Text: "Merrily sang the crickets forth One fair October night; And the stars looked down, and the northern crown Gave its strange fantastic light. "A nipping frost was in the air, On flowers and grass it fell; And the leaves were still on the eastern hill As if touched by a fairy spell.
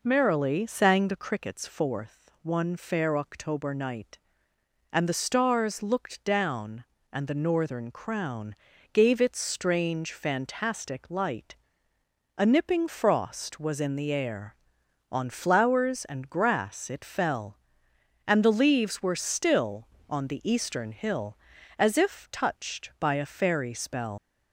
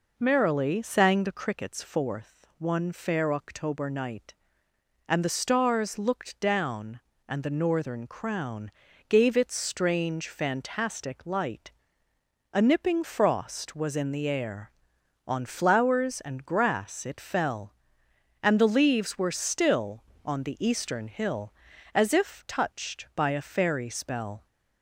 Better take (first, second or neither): second